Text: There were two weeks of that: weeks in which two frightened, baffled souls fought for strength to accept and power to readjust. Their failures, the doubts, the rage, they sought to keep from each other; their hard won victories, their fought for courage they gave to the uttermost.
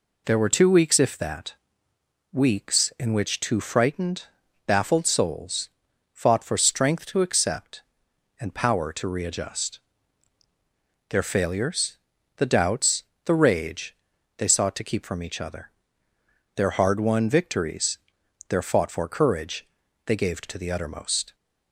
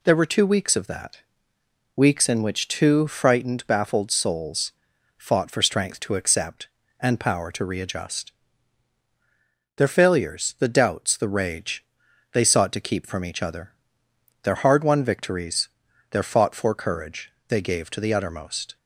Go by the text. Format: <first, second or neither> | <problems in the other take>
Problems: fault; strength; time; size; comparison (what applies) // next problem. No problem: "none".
second | says "if" for "of"; at 0.9 s // pauses between "souls" and "fought"; noticeable; at 5.6 s; 0.46 s long; noticeable in the second // pauses between "courage" and "they"; at 19.6 s; 0.40 s long; slight in the second